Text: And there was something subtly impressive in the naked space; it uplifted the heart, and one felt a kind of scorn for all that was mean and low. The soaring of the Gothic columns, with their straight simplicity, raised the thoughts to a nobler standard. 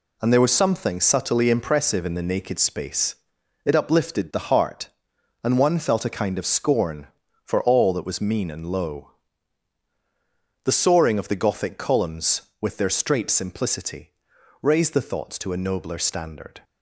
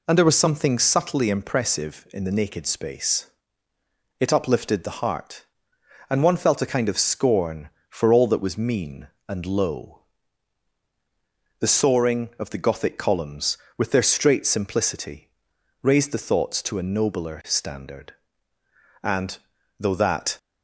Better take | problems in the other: first | goes on to say "And though that"; from 19.0 s on; 1.3 s long

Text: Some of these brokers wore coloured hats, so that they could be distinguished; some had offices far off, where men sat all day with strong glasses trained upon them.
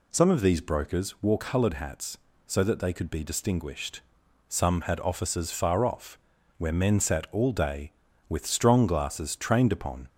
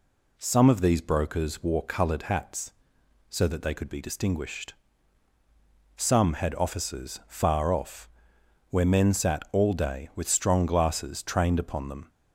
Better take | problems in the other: second | stops before "them"; at 10.0 s

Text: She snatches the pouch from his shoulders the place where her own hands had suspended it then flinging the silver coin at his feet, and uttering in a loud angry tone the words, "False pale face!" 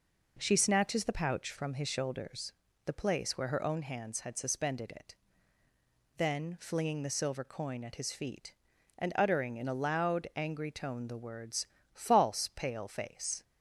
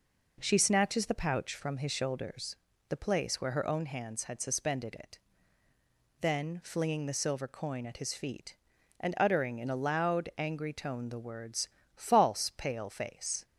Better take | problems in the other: neither | pauses between "shoulders" and "the"; slight; the same in both // pauses between "it" and "then"; the same in both

